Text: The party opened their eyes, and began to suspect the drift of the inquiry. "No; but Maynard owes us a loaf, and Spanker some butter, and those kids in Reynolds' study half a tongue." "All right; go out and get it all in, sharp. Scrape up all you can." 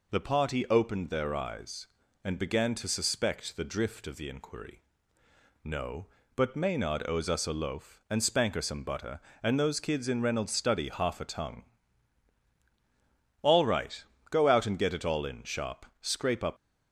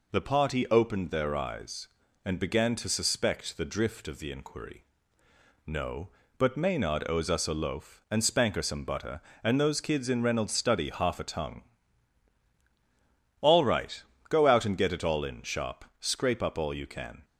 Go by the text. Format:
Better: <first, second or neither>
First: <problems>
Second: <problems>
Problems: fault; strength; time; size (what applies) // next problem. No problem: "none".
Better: second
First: stops before "all you can"; at 16.5 s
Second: none